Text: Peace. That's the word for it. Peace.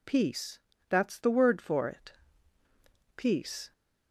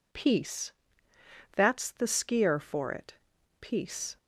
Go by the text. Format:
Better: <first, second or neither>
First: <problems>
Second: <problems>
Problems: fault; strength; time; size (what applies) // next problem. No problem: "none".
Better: first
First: none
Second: says "skier" for "word"; at 2.0 s